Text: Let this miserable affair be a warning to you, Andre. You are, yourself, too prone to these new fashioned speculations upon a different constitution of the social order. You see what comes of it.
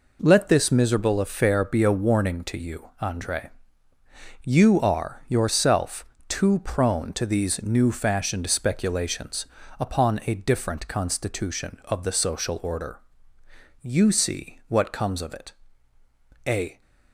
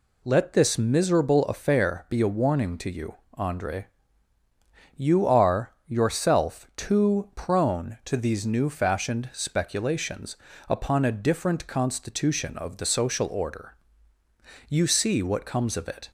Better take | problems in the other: second | pauses between "speculations" and "upon"; slight; at 9.4 s; 0.32 s long; slight in the second // goes on to say "A"; slight; from 16.4 s on; 0.34 s long

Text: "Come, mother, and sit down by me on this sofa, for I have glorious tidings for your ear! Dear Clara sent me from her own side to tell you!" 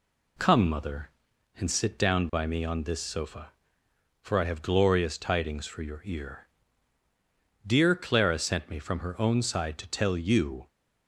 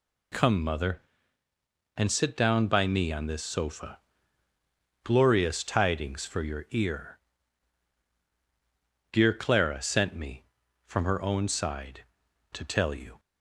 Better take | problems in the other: first | skips "for I have"; at 4.5 s

